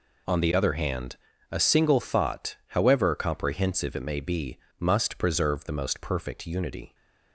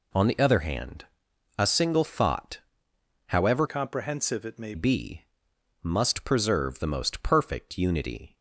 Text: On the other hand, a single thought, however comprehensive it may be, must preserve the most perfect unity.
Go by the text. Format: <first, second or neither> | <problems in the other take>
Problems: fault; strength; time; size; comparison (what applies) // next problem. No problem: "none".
first | changes voice from "comprehensive" to "may"; from 3.6 to 4.7 s; 1.1 s long